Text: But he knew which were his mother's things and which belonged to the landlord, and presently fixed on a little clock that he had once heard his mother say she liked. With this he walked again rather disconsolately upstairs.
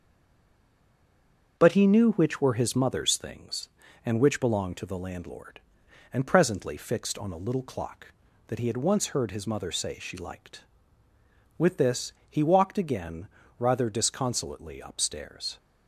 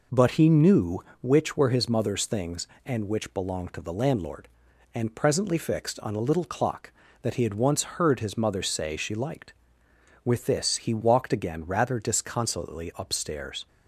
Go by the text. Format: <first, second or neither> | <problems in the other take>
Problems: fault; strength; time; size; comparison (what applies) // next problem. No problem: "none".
second | stays silent before the first word; noticeable; until 1.5 s; 1.5 s long // starts louder than the rest; until 2.5 s; 6.5 dB // pauses between "this" and "he"; slight; at 12.1 s; 0.18 s long // pauses between "again" and "rather"; slight; at 13.2 s; 0.30 s long